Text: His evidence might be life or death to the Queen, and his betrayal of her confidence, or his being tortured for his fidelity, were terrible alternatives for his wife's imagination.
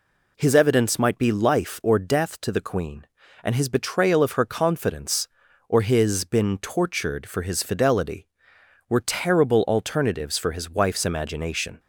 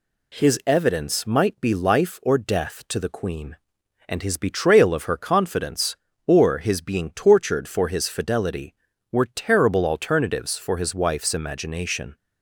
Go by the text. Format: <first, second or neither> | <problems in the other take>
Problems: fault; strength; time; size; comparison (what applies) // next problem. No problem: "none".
second | says "been" for "being"; at 6.2 s